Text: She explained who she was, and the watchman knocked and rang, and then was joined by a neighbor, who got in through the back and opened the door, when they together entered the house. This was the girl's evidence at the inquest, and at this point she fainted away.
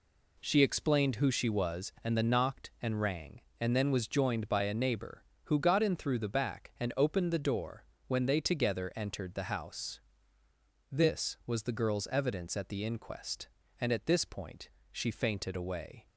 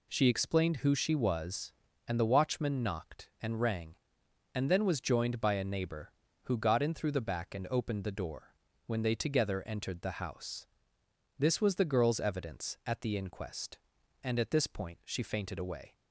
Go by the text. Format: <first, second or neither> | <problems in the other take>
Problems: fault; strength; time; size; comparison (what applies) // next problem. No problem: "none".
second | skips "watchman"; at 2.2 s // pauses between "point" and "she"; slight; at 14.6 s; 0.22 s long